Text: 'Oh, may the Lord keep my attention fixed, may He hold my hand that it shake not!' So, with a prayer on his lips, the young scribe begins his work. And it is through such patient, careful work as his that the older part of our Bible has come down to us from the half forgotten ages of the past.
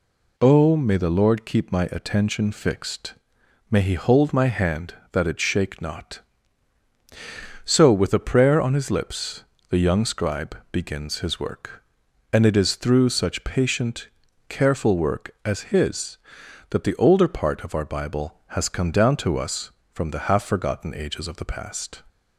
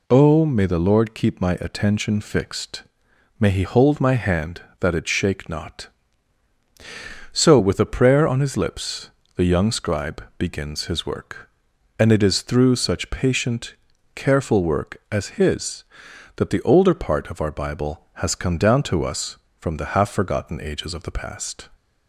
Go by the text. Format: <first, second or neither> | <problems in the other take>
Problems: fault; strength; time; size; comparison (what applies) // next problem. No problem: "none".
neither | none